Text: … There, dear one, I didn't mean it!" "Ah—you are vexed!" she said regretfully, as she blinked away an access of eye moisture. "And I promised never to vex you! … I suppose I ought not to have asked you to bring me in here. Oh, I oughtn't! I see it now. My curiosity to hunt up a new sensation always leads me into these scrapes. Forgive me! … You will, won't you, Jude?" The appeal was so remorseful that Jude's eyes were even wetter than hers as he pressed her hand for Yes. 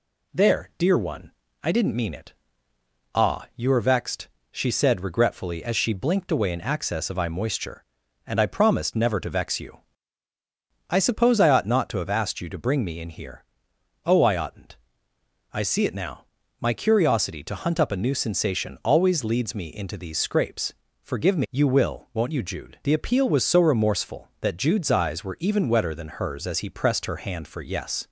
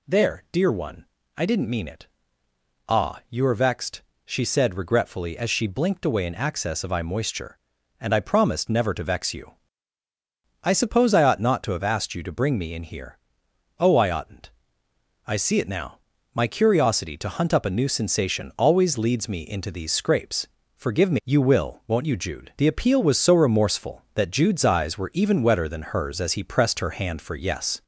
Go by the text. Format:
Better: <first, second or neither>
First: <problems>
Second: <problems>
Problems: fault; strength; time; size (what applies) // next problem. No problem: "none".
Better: first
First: none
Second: gets louder; slight; throughout; 3 dB